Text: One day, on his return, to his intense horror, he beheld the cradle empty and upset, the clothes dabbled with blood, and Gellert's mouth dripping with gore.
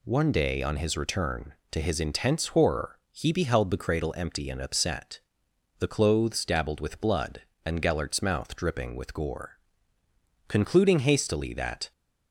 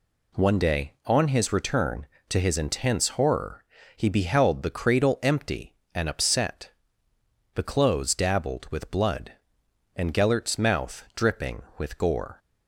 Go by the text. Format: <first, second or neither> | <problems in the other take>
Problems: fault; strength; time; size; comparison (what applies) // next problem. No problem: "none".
second | goes on to say "Concluding hastily that"; from 10.4 s on; 1.4 s long